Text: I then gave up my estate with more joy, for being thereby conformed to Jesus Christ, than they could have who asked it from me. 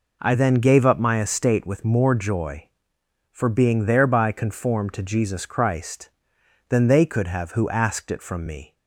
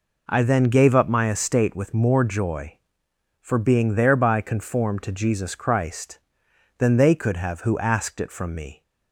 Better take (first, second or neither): neither